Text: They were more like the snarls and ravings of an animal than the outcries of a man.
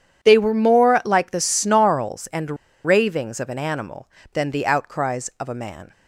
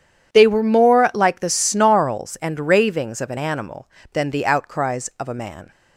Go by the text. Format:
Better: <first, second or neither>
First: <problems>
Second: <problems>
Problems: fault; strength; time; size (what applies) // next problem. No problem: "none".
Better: second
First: starts louder than the rest; strong; until 1.3 s; 9 dB // pauses between "and" and "ravings"; slight; at 2.5 s; 0.29 s long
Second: none